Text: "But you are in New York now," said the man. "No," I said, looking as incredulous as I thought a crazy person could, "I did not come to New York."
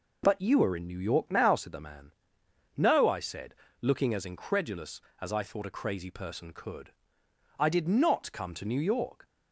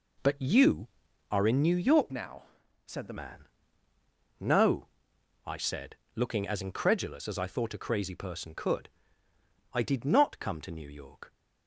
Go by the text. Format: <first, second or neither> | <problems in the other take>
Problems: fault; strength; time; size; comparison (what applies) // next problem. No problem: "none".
first | changes voice from "now" to "the"; from 2.1 to 3.1 s; 1.0 s long